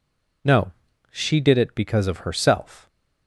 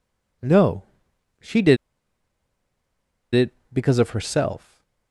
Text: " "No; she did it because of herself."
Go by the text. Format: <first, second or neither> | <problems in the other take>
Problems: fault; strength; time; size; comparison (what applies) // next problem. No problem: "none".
first | pauses between "did" and "it"; strong; at 1.7 s; 1.5 s long // stays silent after the last word; slight; from 4.5 s on; 0.6 s long